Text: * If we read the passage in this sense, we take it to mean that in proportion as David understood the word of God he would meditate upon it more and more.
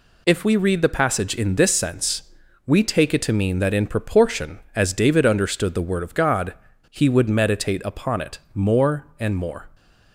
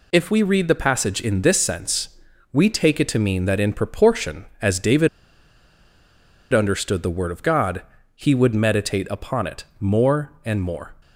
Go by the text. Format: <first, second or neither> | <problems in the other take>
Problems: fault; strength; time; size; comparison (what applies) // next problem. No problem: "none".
first | pauses between "David" and "understood"; strong; at 5.0 s; 1.4 s long // pauses between "God" and "he"; slight; at 7.8 s; 0.32 s long; slight in the first // pauses between "it" and "more"; slight; at 9.6 s; 0.16 s long; slight in the first